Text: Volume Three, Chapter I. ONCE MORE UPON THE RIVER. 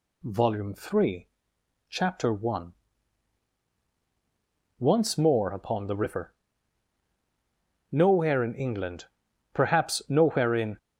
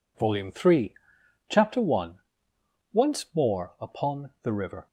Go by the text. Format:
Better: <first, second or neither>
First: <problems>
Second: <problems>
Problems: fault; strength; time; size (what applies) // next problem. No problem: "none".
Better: second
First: goes on to say "Nowhere in England perhaps nowhere in"; strong; from 7.9 s on; 2.8 s long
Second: none